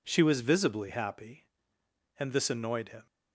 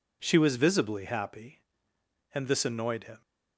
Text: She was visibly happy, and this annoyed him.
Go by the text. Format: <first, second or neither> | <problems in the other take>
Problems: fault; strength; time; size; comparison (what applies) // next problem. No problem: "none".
neither | none